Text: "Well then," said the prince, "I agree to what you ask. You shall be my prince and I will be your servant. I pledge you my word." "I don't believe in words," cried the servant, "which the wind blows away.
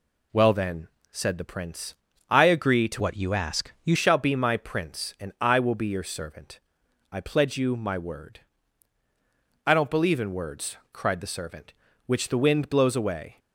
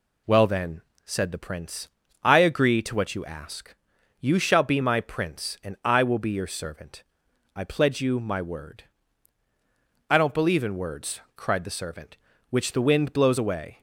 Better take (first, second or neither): second